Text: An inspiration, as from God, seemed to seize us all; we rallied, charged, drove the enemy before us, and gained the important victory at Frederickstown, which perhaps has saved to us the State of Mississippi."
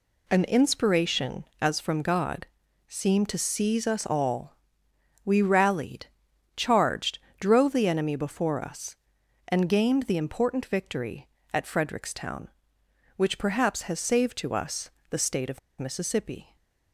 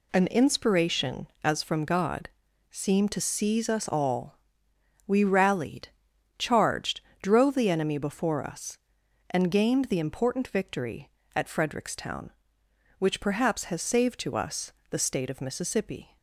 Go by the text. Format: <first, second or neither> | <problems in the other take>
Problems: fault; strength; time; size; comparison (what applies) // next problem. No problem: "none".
second | pauses between "us" and "the"; slight; at 14.8 s; 0.22 s long; slight in the second // pauses between "of" and "Mississippi"; slight; at 15.5 s; 0.20 s long